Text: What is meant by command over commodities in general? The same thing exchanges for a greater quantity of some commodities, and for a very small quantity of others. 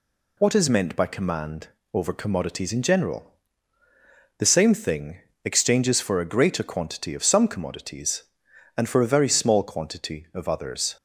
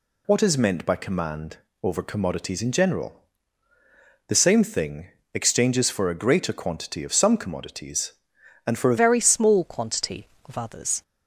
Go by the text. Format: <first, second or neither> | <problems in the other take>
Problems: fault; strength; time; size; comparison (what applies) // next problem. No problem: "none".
first | pauses between "command" and "over"; slight; at 1.5 s; 0.26 s long; slight in the first // pauses between "thing" and "exchanges"; slight; at 5.0 s; 0.28 s long; slight in the first // changes voice at "very"; from 8.9 s on; 2.1 s long